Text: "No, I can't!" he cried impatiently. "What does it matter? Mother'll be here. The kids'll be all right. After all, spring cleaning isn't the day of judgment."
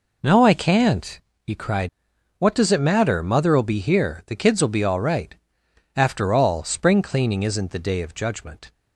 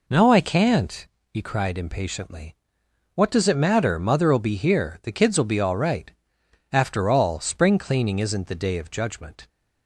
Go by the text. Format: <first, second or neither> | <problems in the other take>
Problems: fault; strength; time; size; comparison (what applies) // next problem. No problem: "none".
second | skips "impatiently"; at 2.1 s